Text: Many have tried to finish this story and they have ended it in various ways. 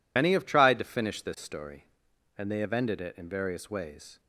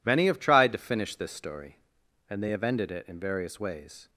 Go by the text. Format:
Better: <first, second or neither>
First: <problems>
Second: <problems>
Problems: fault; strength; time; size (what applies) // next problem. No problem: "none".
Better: second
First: loses the start of "Many"; at 0.1 s; 60 ms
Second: none